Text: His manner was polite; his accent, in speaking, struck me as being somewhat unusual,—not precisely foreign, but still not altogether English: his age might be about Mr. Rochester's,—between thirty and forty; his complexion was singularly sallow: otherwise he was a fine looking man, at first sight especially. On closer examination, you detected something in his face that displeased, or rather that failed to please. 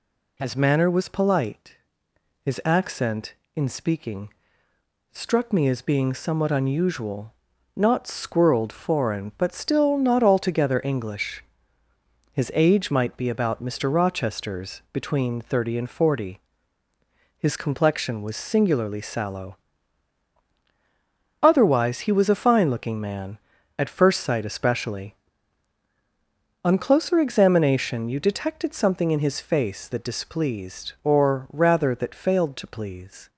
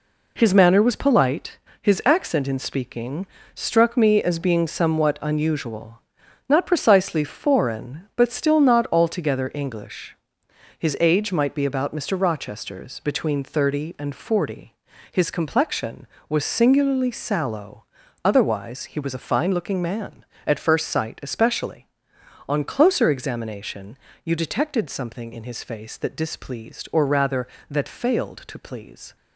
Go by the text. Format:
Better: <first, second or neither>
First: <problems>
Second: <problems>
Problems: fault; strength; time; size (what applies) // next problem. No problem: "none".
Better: second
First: says "squirreled" for "precisely"; at 8.0 s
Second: none